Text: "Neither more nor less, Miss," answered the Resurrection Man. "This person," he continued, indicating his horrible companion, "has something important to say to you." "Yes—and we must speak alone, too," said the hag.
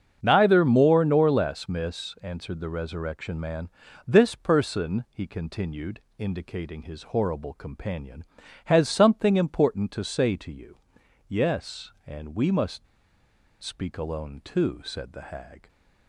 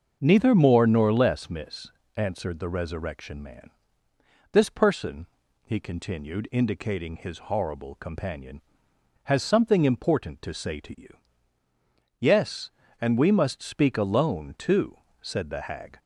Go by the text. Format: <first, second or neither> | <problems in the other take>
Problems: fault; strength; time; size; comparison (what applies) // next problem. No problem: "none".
second | starts louder than the rest; strong; until 1.2 s; 7.5 dB; also in the second // pauses between "must" and "speak"; noticeable; at 12.8 s; 0.78 s long